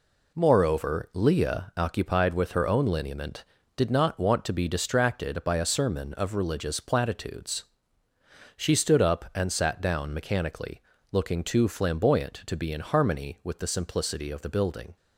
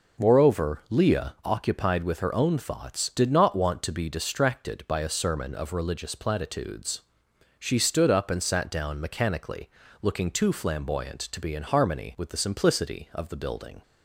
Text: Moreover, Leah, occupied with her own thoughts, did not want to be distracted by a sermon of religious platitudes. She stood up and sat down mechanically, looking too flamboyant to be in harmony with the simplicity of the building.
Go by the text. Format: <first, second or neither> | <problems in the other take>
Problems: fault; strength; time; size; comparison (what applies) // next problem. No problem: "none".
second | says "lineament" for "thoughts"; at 2.8 s